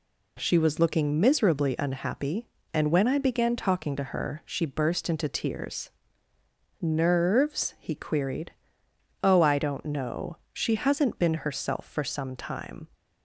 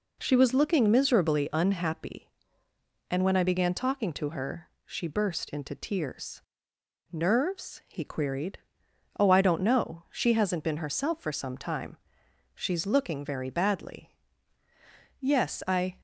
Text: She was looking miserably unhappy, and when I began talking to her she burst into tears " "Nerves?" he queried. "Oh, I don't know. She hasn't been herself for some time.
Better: first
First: none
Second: pauses between "her" and "she"; slight; at 4.6 s; 0.18 s long // goes on to say "She's looking very badly Yes I"; strong; from 12.5 s on; 3.4 s long

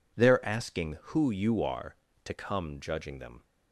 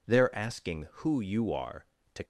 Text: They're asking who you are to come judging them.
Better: first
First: none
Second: stops before "come judging them"; at 2.2 s

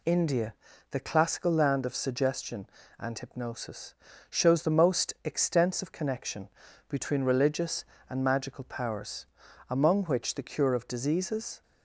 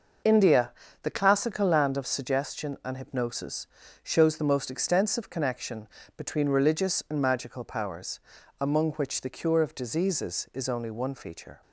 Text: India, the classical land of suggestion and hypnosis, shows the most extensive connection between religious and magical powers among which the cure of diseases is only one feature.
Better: second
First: pauses between "connection" and "between"; at 6.4 s; 0.40 s long // pauses between "powers" and "among"; at 9.2 s; 0.44 s long // stops before "is only one feature"; at 11.6 s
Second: pauses between "connection" and "between"; slight; at 5.8 s; 0.30 s long // pauses between "powers" and "among"; at 8.1 s; 0.40 s long

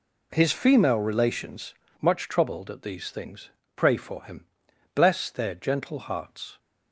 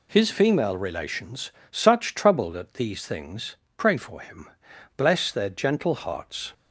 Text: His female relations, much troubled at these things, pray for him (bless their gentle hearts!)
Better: first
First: none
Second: says "such" for "much"; at 1.6 s

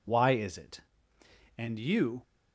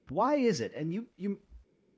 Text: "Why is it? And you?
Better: first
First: none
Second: says "you" twice; at 1.1 s

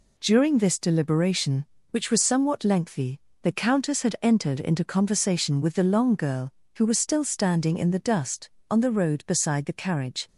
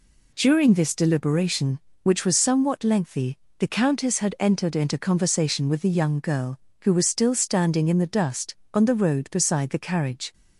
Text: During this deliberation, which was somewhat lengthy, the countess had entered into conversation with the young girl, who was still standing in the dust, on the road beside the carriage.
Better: second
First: says "long" for "young"; at 5.8 s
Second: none

